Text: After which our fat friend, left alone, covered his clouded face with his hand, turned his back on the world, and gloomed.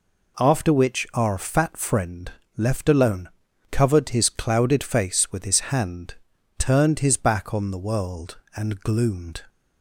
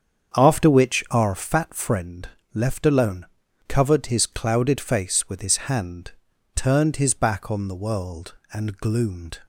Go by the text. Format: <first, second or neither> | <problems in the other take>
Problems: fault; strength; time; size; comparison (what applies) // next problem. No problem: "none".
first | starts louder than the rest; strong; until 1.5 s; 7.5 dB